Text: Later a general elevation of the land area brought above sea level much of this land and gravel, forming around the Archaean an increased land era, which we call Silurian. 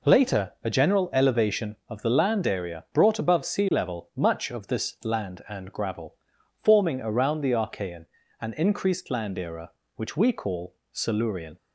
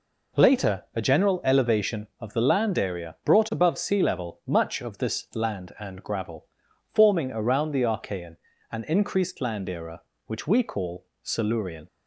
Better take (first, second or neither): neither